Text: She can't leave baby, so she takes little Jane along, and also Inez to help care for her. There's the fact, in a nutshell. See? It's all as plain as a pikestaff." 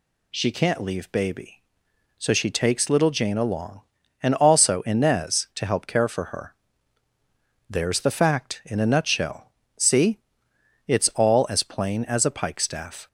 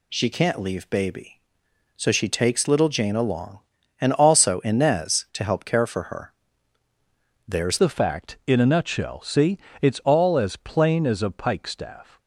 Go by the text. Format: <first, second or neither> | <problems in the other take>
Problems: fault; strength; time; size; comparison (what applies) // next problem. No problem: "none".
first | changes voice at "the"; from 7.7 s on; 4.4 s long